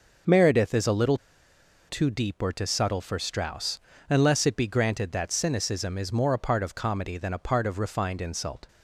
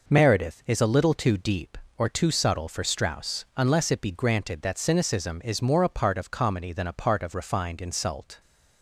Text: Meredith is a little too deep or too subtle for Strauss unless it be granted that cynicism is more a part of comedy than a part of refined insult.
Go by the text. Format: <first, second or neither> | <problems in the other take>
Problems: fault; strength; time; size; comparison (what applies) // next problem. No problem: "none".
second | pauses between "little" and "too"; noticeable; at 1.1 s; 0.70 s long // pauses between "Strauss" and "unless"; slight; at 3.7 s; 0.28 s long